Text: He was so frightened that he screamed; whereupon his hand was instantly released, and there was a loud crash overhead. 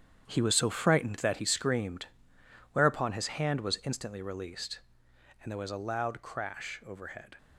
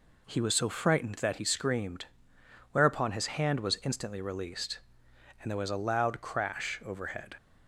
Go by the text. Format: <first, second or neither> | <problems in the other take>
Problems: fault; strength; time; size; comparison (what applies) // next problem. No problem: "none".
second | gets quieter; strong; throughout; 10.5 dB